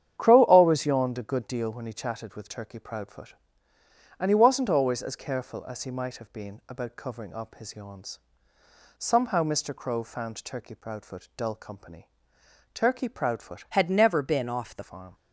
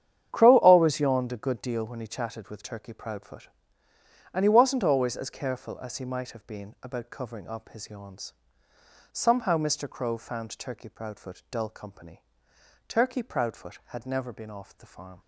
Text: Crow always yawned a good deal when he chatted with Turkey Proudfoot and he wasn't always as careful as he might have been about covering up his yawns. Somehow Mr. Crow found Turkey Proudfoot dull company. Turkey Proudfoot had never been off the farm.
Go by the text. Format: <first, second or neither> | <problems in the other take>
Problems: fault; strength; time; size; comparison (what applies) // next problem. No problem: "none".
second | starts louder than the rest; strong; until 1.2 s; 9 dB; strong in the second // changes voice from "had" to "the"; from 13.6 to 14.8 s; 1.2 s long